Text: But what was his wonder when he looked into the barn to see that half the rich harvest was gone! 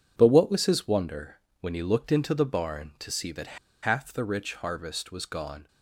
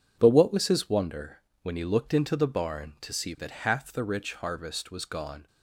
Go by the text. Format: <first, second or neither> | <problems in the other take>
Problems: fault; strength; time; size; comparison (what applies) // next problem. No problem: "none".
second | pauses between "wonder" and "when"; slight; at 1.3 s; 0.24 s long; slight in the second // pauses between "that" and "half"; slight; at 3.5 s; 0.27 s long